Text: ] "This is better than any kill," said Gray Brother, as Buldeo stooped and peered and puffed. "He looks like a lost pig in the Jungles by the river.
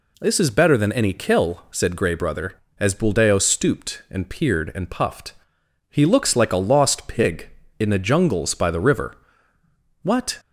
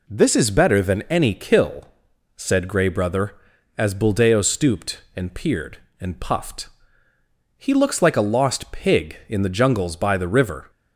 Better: second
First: goes on to say "What"; slight; from 10.0 s on; 0.36 s long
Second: none

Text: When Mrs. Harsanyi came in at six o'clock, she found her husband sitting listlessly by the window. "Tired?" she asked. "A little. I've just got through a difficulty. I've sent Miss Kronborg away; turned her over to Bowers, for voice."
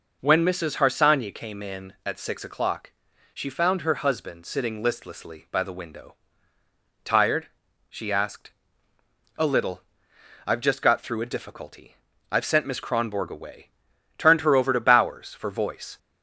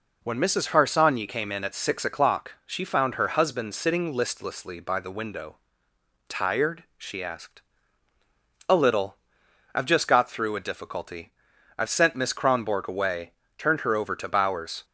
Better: first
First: none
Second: stops before "for voice"; at 14.8 s

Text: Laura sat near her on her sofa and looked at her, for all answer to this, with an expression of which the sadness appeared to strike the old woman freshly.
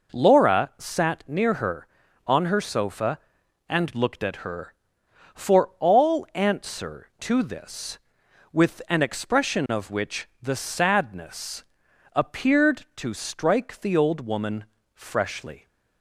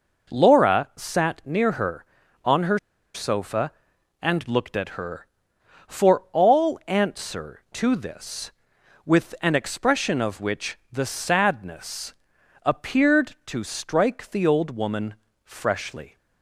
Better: first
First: pauses between "sadness" and "appeared"; noticeable; at 11.6 s; 0.50 s long // pauses between "woman" and "freshly"; slight; at 14.6 s; 0.30 s long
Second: pauses between "her" and "sofa"; slight; at 2.7 s; 0.35 s long // pauses between "sadness" and "appeared"; noticeable; at 12.1 s; 0.50 s long // pauses between "woman" and "freshly"; slight; at 15.1 s; 0.30 s long

